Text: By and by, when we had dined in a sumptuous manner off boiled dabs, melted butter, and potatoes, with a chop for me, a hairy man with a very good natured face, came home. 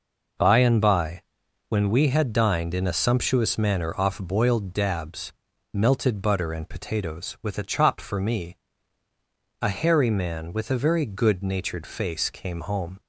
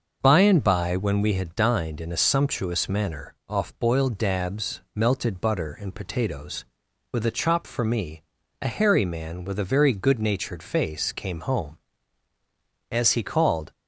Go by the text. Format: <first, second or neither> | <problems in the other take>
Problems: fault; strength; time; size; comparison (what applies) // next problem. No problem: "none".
first | starts louder than the rest; noticeable; until 1.2 s; 6 dB // goes on to say "As he called"; noticeable; from 12.9 s on; 0.80 s long